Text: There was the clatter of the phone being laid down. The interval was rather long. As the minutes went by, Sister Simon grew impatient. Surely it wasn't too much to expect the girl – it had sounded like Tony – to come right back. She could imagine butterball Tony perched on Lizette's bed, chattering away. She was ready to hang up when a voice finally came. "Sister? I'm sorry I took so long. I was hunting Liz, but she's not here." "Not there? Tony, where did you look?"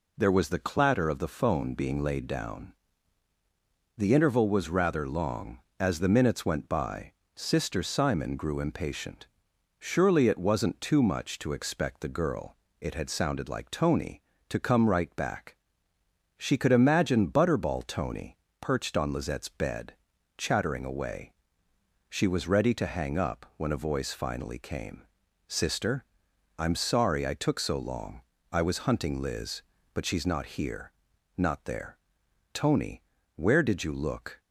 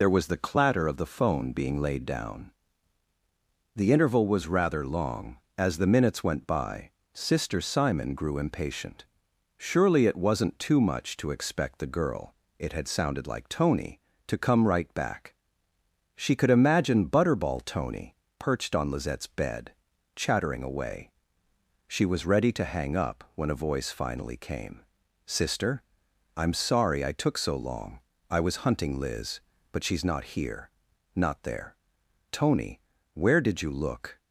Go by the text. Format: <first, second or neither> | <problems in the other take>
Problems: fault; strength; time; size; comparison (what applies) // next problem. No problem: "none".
first | loses the start of "There"; at 0.0 s; 55 ms // pauses between "Tony" and "perched"; slight; at 18.1 s; 0.24 s long; slight in the first